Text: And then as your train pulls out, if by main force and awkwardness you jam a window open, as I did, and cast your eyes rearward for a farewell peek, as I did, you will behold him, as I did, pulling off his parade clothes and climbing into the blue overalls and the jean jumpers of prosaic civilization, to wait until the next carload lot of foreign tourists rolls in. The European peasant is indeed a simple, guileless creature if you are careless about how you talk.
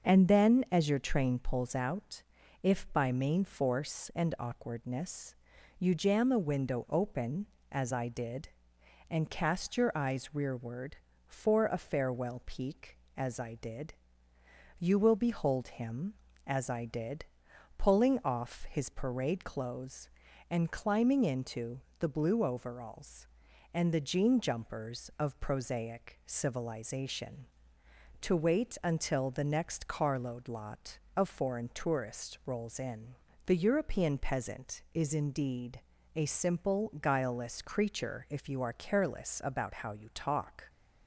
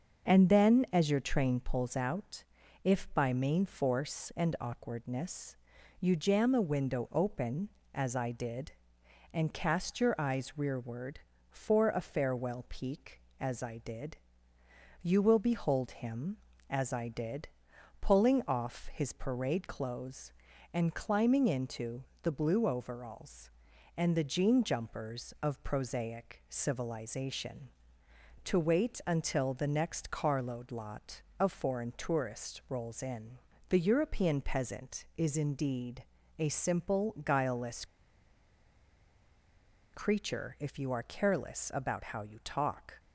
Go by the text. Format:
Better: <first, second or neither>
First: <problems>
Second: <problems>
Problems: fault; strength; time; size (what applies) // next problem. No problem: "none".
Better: first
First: starts louder than the rest; until 1.1 s; 6.5 dB // pauses between "awkwardness" and "you"; noticeable; at 5.3 s; 0.46 s long // pauses between "into" and "the"; slight; at 21.7 s; 0.20 s long // pauses between "indeed" and "a"; slight; at 35.7 s; 0.36 s long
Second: starts louder than the rest; until 1.3 s; 6.5 dB // pauses between "awkwardness" and "you"; noticeable; at 5.5 s; 0.46 s long // pauses between "into" and "the"; slight; at 22.0 s; 0.20 s long // pauses between "indeed" and "a"; slight; at 36.0 s; 0.36 s long // pauses between "guileless" and "creature"; strong; at 37.8 s; 2.0 s long